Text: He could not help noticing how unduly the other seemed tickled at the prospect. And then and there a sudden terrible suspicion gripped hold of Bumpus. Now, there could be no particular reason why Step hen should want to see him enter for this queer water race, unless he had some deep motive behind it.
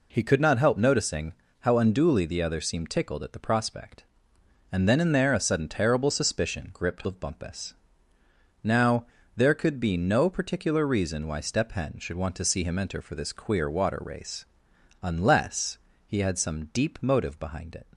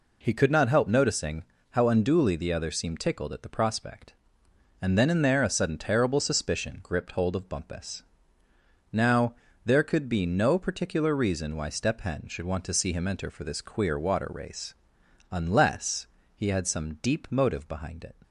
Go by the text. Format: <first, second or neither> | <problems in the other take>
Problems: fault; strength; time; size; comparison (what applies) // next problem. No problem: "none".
second | pauses between "noticing" and "how"; slight; at 1.3 s; 0.30 s long; slight in the second // skips "hold"; at 7.0 s // pauses between "unless" and "he"; slight; at 15.7 s; 0.28 s long; slight in the second